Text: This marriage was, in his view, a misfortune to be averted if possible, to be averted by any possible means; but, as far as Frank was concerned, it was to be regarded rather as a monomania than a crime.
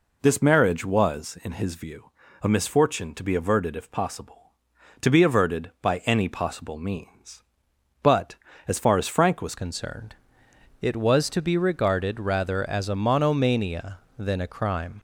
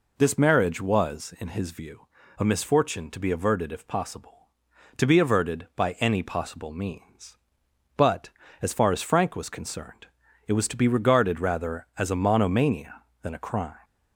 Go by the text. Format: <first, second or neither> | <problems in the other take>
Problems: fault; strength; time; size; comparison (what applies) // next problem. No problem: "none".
second | changes voice at "concerned"; from 9.5 s on; 5.4 s long